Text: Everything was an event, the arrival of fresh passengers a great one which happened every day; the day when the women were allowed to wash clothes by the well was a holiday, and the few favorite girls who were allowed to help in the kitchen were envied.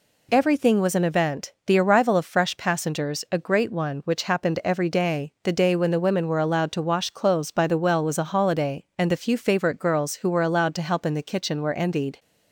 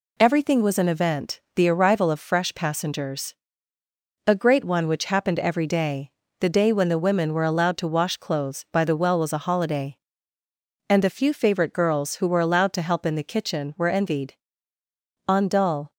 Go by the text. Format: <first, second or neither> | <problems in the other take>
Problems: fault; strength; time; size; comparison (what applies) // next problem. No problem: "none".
first | pauses between "passengers" and "a"; noticeable; at 3.3 s; 0.94 s long // goes on to say "On dull"; noticeable; from 15.2 s on; 0.64 s long